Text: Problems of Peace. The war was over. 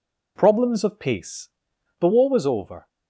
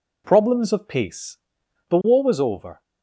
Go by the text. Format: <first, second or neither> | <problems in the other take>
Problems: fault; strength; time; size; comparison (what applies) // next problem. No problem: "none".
neither | none